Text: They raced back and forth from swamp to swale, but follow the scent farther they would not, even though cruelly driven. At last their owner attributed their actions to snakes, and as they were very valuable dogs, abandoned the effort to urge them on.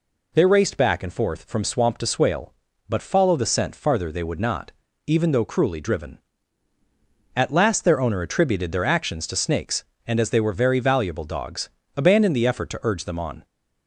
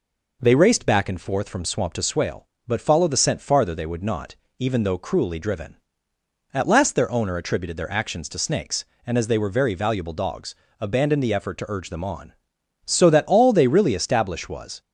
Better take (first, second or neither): first